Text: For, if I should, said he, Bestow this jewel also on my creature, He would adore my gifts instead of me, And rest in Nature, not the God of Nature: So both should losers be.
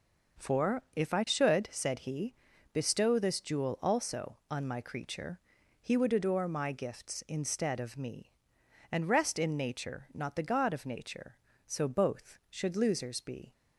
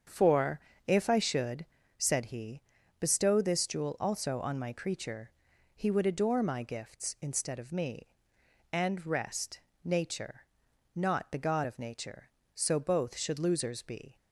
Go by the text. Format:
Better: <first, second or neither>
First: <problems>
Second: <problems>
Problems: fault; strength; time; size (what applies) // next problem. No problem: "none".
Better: first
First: none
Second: starts louder than the rest; strong; until 1.3 s; 7.5 dB // skips "in"; at 9.7 s